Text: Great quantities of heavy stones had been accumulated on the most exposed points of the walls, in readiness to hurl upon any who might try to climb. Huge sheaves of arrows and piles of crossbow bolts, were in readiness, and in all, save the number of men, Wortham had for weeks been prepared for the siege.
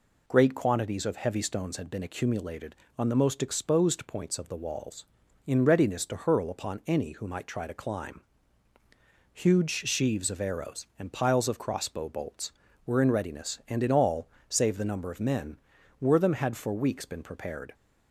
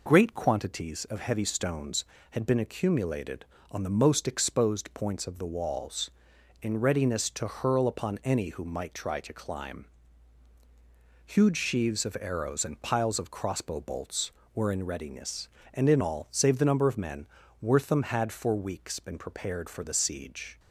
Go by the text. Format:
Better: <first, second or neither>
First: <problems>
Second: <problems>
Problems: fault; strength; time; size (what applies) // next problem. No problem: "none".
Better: second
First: stops before "for the siege"; at 17.7 s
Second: none